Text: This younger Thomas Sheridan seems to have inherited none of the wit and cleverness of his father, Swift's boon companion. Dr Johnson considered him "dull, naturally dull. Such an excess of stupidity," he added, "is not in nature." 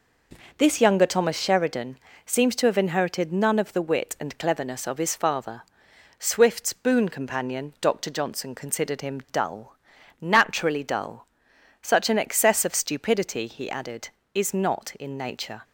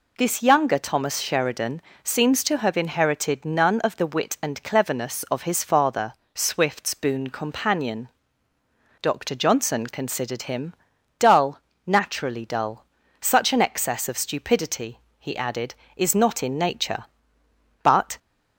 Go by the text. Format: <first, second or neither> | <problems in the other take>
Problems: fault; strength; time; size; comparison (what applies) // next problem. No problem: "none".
first | pauses between "Sheridan" and "seems"; slight; at 1.8 s; 0.22 s long; slight in the first // pauses between "him" and "dull"; at 10.7 s; 0.44 s long // goes on to say "But"; slight; from 17.8 s on; 0.34 s long